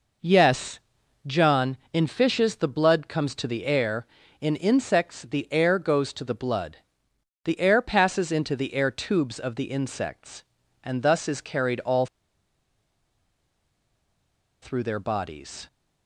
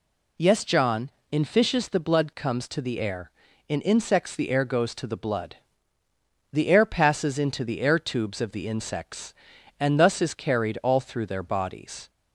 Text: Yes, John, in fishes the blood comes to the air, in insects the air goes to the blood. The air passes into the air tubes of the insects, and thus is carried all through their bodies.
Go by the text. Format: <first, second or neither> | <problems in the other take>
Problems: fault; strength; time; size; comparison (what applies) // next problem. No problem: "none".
second | pauses between "all" and "through"; strong; at 12.0 s; 2.5 s long